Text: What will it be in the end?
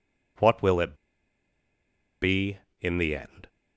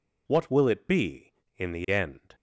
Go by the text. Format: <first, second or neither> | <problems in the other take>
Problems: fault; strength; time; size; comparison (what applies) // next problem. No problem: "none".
second | pauses between "it" and "be"; strong; at 0.9 s; 1.2 s long